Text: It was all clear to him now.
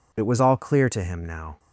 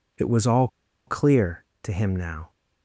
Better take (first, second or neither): first